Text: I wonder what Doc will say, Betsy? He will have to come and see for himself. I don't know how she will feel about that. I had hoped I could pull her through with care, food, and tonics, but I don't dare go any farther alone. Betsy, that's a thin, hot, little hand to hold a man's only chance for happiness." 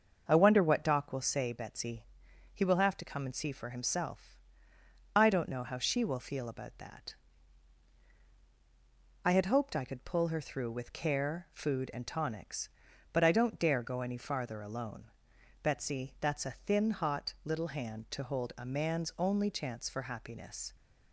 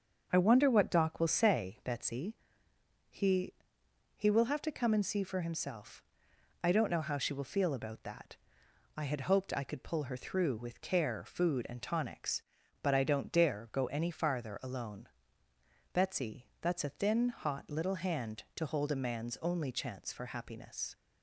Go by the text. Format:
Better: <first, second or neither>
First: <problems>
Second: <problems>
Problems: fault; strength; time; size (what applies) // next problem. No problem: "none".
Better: first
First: starts louder than the rest; until 1.2 s; 6.5 dB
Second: starts louder than the rest; until 1.3 s; 6.5 dB // says "He" twice; at 4.1 s